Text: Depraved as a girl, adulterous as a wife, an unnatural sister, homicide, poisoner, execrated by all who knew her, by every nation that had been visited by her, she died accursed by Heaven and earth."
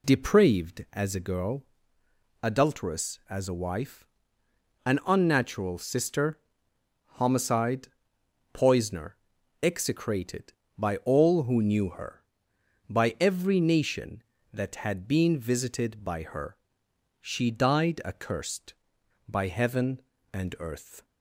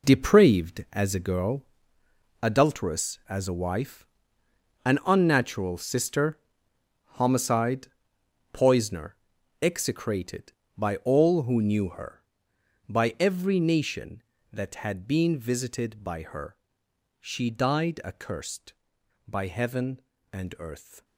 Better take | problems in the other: first | gets quieter; strong; throughout; 11 dB

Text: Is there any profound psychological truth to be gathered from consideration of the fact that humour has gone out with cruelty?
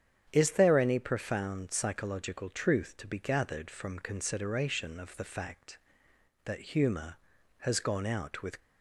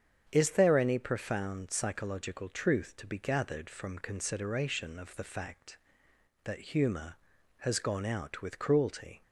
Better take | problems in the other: second | starts louder than the rest; strong; until 1.3 s; 8.5 dB; strong in the second // stops before "cruelty"; at 8.5 s

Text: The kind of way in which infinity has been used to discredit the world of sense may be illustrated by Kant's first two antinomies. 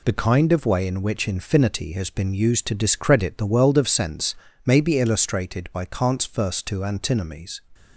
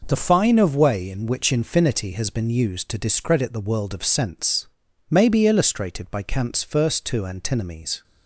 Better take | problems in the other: first | says "fine" for "kind"; at 0.1 s // pauses between "sense" and "may"; at 4.6 s; 0.42 s long; slight in the first

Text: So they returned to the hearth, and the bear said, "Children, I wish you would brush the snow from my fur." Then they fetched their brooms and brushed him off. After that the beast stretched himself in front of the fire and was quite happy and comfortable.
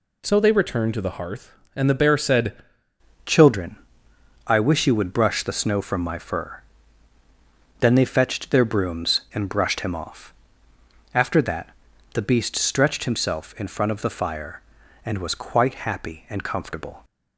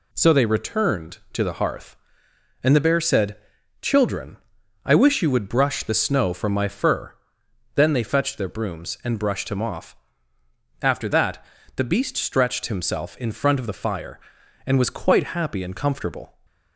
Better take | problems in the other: second | changes voice at "Children"; from 3.2 s on; 13.8 s long // pauses between "that" and "the"; at 11.7 s; 0.44 s long; slight in the second

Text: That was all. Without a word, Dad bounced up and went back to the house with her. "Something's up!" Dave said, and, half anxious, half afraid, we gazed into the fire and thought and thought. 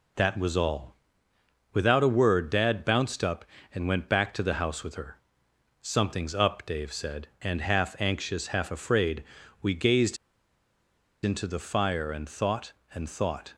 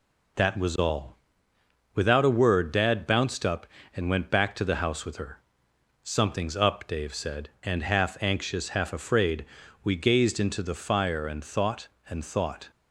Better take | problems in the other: second | pauses between "gazed" and "into"; at 10.1 s; 1.0 s long

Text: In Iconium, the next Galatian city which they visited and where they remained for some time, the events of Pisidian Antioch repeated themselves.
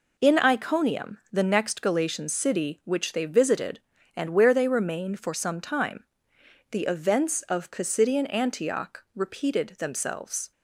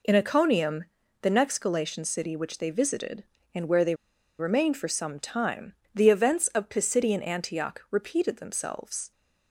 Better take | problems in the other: first | pauses between "they" and "remained"; at 3.9 s; 0.44 s long

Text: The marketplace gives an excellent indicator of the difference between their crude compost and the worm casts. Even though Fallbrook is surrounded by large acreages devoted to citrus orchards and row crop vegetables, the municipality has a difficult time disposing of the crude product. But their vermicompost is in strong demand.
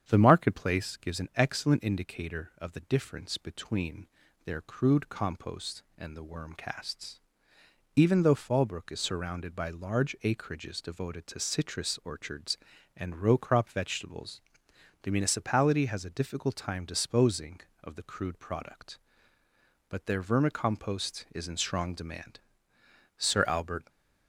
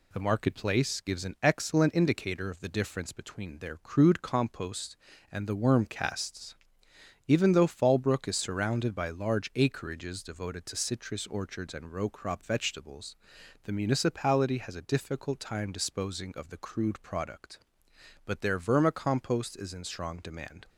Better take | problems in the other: second | starts louder than the rest; strong; until 1.0 s; 8.5 dB // pauses between "between" and "their"; at 4.0 s; 0.38 s long // goes on to say "Sir Albert"; noticeable; from 23.1 s on; 0.70 s long

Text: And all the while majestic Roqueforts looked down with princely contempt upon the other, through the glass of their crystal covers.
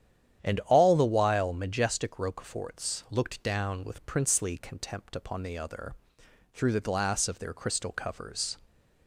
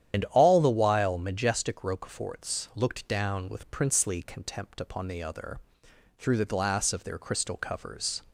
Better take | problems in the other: first | loses the start of "And"; at 0.1 s; 90 ms // starts louder than the rest; strong; until 1.1 s; 10 dB; strong in the first

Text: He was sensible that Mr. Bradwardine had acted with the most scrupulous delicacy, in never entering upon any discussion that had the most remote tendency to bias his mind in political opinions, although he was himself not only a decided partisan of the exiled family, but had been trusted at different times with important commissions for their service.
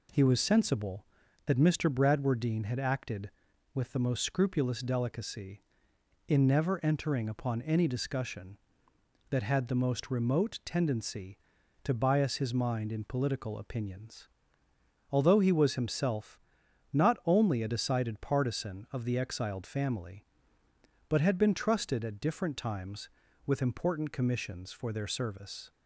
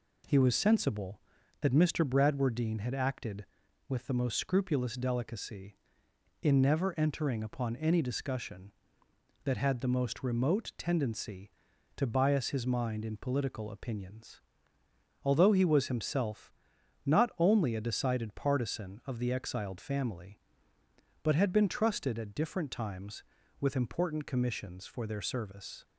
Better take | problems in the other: neither | pauses between "himself" and "not"; noticeable; the same in both

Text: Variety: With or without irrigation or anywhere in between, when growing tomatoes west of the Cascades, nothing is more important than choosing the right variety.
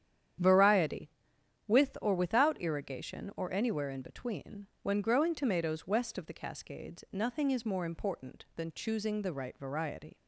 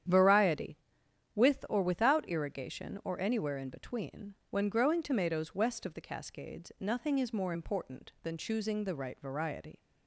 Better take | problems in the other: neither | starts louder than the rest; strong; the same in both

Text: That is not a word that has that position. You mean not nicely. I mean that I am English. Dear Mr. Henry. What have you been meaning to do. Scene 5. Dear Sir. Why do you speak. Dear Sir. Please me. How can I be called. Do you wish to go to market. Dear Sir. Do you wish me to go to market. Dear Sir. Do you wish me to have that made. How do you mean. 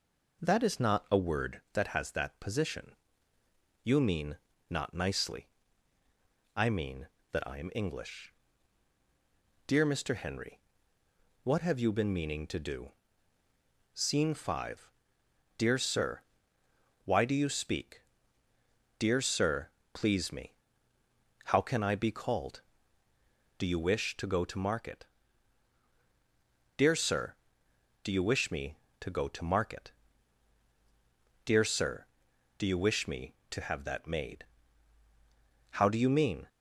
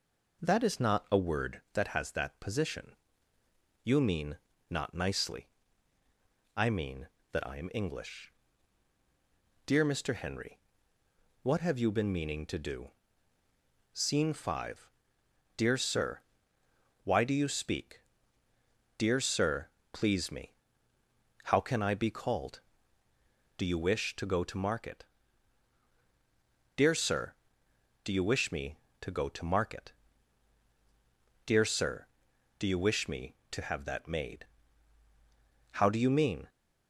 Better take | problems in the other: neither | pauses between "mean" and "not"; slight; the same in both

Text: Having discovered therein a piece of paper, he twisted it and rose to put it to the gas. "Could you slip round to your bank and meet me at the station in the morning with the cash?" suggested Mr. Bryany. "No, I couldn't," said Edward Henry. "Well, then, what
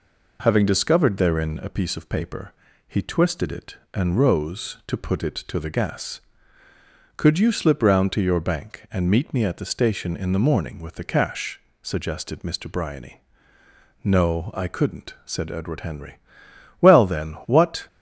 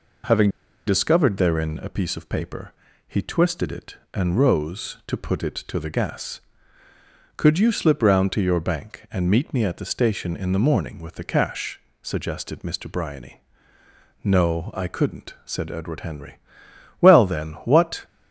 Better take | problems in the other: first | pauses between "Having" and "discovered"; at 0.4 s; 0.38 s long

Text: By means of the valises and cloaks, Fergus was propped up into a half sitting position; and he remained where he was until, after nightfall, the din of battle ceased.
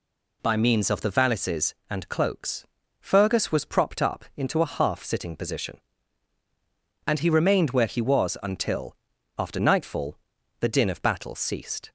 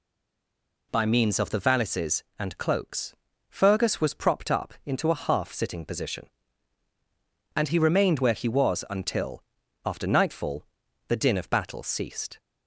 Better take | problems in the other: first | stays silent before the first word; slight; until 0.9 s; 0.9 s long

